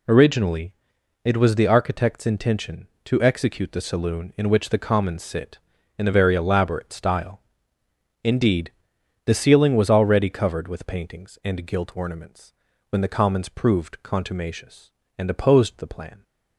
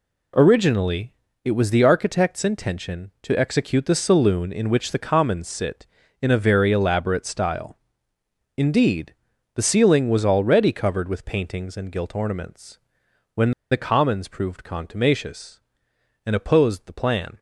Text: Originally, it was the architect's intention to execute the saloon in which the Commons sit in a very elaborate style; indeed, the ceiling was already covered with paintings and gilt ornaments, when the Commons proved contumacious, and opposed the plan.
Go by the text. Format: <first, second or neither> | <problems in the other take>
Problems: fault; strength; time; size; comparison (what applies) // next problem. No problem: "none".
first | pauses between "when" and "the"; slight; at 13.5 s; 0.19 s long